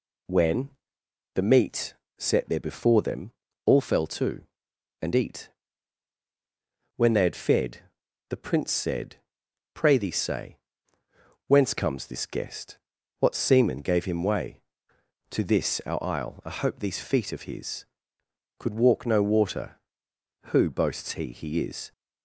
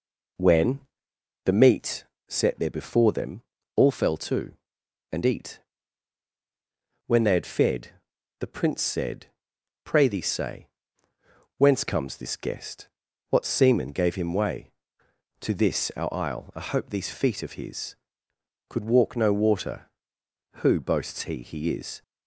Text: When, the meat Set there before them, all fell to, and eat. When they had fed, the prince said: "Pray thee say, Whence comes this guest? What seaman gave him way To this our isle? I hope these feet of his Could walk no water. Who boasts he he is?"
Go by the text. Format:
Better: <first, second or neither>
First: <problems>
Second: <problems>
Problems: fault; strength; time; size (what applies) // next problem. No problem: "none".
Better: first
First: pauses between "meat" and "Set"; slight; at 1.9 s; 0.24 s long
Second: starts louder than the rest; until 1.9 s; 3.5 dB // pauses between "meat" and "Set"; slight; at 2.0 s; 0.24 s long